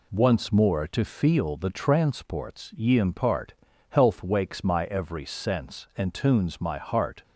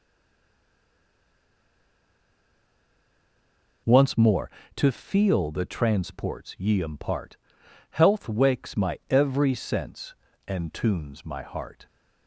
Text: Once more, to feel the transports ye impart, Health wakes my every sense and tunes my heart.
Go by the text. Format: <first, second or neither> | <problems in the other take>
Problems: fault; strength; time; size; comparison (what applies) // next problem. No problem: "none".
first | stays silent before the first word; strong; until 3.8 s; 3.8 s long